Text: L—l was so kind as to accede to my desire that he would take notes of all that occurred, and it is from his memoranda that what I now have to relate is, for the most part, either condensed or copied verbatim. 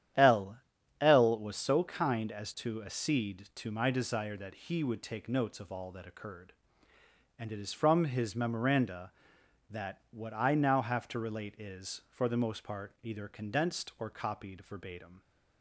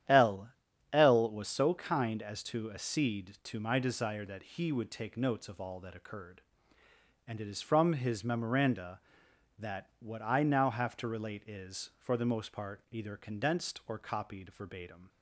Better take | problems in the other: neither | starts louder than the rest; strong; the same in both

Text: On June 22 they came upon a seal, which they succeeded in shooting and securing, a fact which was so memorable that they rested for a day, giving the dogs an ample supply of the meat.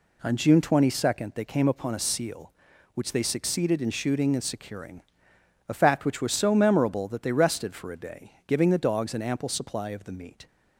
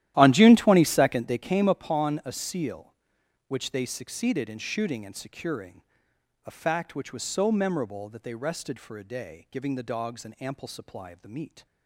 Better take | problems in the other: first | starts louder than the rest; strong; until 1.5 s; 13 dB

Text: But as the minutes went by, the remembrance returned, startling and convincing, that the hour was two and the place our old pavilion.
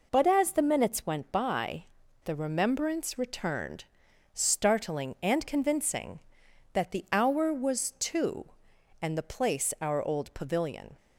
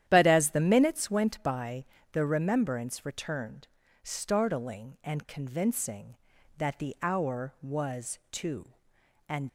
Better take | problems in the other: first | starts louder than the rest; strong; until 1.0 s; 11 dB // stops before "the place our old pavilion"; at 9.4 s

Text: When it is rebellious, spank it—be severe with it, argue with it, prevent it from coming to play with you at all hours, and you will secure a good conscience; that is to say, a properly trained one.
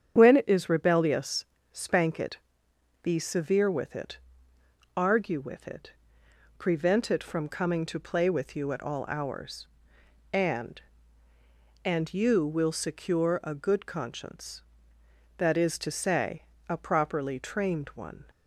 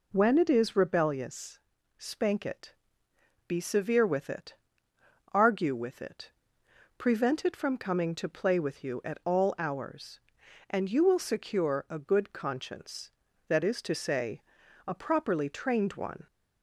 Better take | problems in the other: second | starts louder than the rest; strong; until 1.1 s; 8.5 dB // says "and" twice; at 11.8 s

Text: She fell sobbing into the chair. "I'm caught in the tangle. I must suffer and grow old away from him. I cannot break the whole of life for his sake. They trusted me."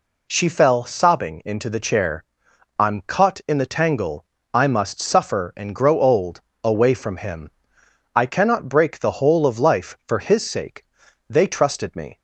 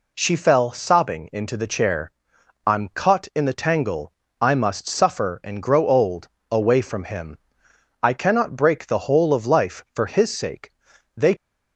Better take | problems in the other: first | pauses between "old" and "away"; slight; at 6.2 s; 0.22 s long; slight in the first // stops before "trusted me"; at 11.3 s

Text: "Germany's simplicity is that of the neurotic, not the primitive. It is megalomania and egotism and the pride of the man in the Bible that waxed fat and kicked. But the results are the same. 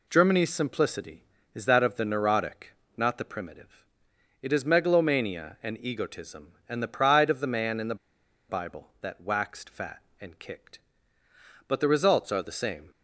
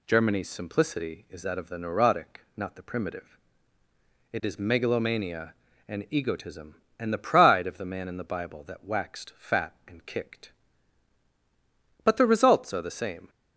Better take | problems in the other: second | pauses between "the" and "Bible"; noticeable; at 7.9 s; 0.53 s long

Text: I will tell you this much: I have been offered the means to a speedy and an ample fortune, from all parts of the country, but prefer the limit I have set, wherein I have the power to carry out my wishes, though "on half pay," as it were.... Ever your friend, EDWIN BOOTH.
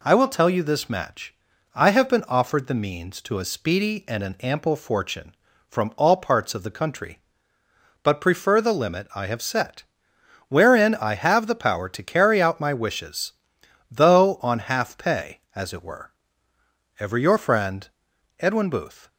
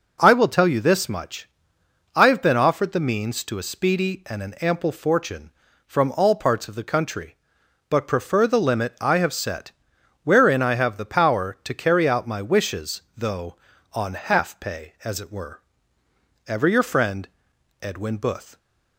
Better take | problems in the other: second | says "match" for "much"; at 0.8 s

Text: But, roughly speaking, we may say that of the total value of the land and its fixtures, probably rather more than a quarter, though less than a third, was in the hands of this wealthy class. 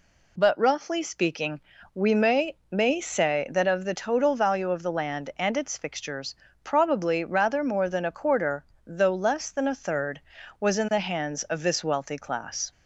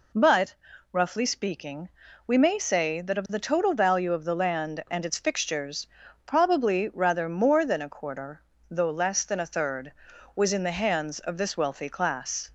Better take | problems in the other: second | says "may" twice; at 2.7 s

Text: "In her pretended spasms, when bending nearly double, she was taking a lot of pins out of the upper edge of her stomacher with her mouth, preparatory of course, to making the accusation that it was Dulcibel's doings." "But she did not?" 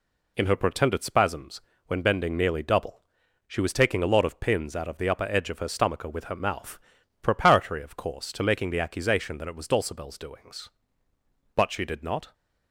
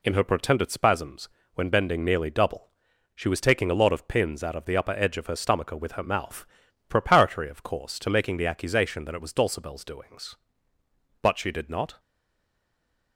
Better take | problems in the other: first | stays silent after the last word; noticeable; from 11.9 s on; 1.2 s long

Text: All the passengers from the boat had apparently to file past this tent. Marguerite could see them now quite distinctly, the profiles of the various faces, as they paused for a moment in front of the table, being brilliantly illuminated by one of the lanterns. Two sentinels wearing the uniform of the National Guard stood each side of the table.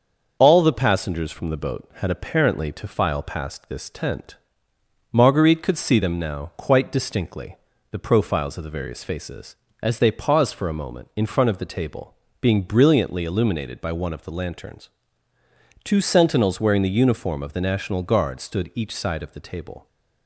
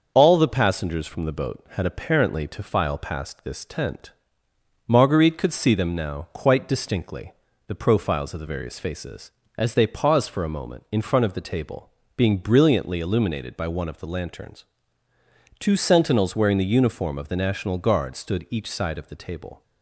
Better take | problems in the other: neither | starts louder than the rest; the same in both

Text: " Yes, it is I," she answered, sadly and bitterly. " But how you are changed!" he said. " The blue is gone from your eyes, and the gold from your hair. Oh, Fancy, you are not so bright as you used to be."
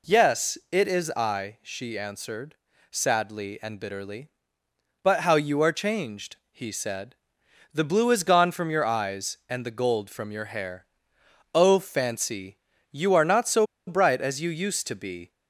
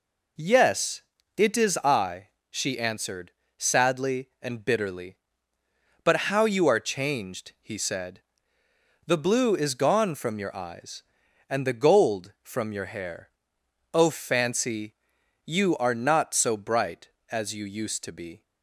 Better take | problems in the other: second | pauses between "so" and "bright"; slight; at 13.6 s; 0.22 s long

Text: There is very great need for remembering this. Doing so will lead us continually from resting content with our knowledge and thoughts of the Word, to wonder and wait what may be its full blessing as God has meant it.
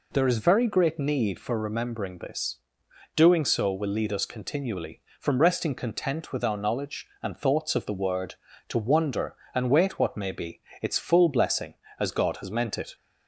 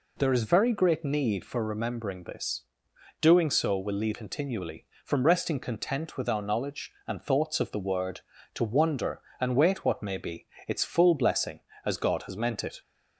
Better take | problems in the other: first | skips "us"; at 4.1 s // pauses between "be" and "its"; slight; at 10.4 s; 0.20 s long; slight in the first

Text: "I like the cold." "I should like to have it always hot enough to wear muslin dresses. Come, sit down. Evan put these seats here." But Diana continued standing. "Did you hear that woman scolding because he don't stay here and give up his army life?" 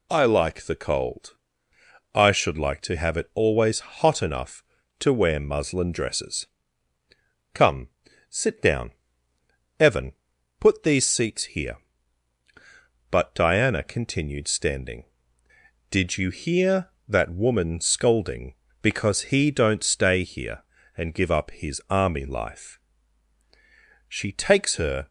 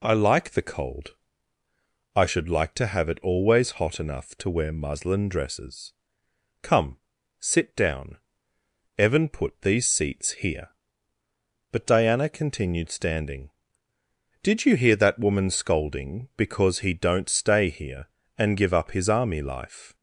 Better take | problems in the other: second | pauses between "Evan" and "put"; noticeable; at 10.1 s; 0.48 s long // goes on to say "She takes her"; noticeable; from 24.0 s on; 1.0 s long

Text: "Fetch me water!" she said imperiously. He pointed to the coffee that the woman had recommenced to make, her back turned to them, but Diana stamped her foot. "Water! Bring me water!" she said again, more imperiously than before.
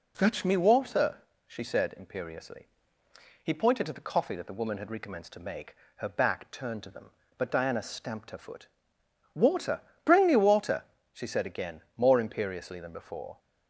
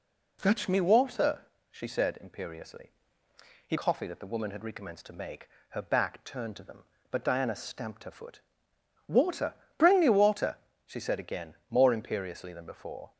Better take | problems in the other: first | skips "pointed to the"; at 3.7 s

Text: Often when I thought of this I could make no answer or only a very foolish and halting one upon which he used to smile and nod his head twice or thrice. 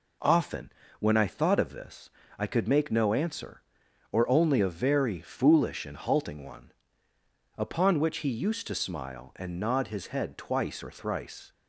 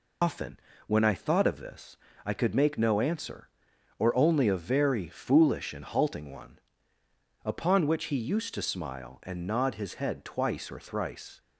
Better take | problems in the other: first | loses the start of "Often"; at 0.2 s; 135 ms // pauses between "Often" and "when"; slight; at 0.5 s; 0.28 s long; slight in the first // pauses between "this" and "I"; slight; at 1.9 s; 0.28 s long; slight in the first // pauses between "one" and "upon"; noticeable; at 6.5 s; 0.86 s long; noticeable in the first

